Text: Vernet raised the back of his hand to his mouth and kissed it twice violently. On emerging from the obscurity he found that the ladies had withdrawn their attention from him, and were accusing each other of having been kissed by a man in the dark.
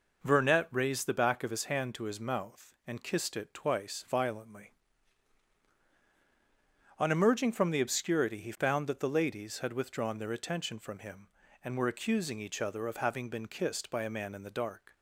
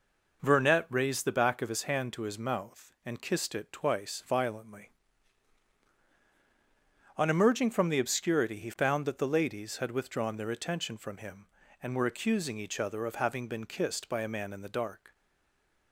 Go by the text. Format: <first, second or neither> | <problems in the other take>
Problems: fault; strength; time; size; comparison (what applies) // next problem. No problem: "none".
first | stays silent after the last word; slight; from 15.1 s on; 0.8 s long